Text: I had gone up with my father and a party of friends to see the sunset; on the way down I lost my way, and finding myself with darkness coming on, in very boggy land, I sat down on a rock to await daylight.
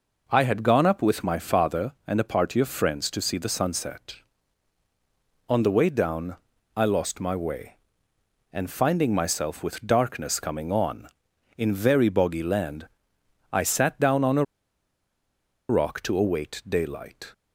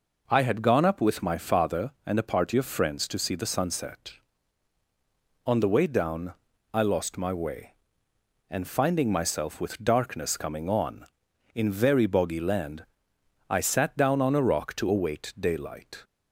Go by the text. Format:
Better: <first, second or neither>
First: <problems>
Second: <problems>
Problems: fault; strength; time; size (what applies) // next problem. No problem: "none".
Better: second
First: pauses between "down" and "I"; at 6.3 s; 0.40 s long // pauses between "a" and "rock"; strong; at 14.4 s; 1.2 s long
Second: pauses between "down" and "I"; at 6.3 s; 0.40 s long